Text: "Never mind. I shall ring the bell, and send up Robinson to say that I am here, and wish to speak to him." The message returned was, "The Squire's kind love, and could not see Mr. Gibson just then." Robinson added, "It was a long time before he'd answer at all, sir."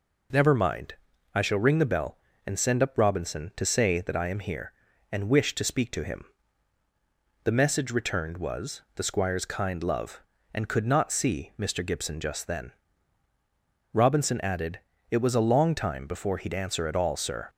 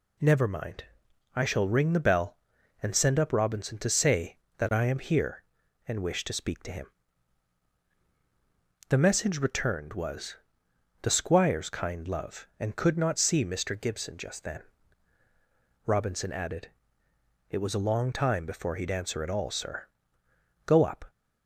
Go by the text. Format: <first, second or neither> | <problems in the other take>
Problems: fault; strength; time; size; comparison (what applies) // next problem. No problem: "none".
first | goes on to say "Go up"; slight; from 20.6 s on; 0.44 s long